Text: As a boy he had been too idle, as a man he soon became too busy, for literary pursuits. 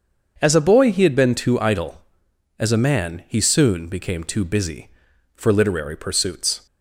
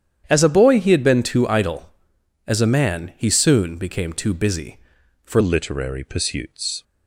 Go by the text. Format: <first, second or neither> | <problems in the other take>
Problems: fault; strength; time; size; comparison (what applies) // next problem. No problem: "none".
first | starts louder than the rest; strong; until 1.2 s; 9.5 dB; also in the first // changes voice at "literary"; from 5.4 s on; 1.4 s long